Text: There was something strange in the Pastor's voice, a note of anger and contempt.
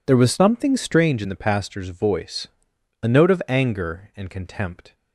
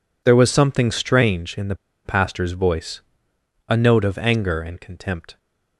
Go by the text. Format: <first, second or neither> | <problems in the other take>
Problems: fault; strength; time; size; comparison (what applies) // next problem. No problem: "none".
first | pauses between "the" and "Pastor's"; slight; at 1.7 s; 0.29 s long